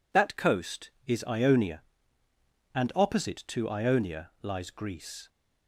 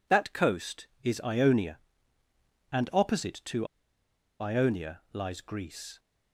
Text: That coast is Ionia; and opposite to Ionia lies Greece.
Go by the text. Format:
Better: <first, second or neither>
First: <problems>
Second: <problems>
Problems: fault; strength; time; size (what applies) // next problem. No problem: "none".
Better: first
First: none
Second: pauses between "to" and "Ionia"; noticeable; at 3.6 s; 0.74 s long